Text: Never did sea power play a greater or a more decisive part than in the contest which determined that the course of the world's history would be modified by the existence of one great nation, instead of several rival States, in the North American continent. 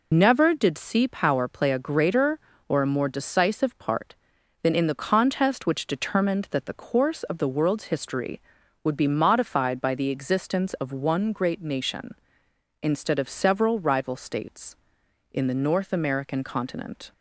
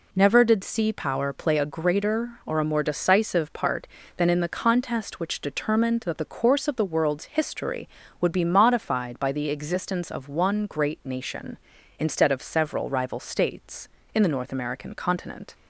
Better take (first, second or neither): second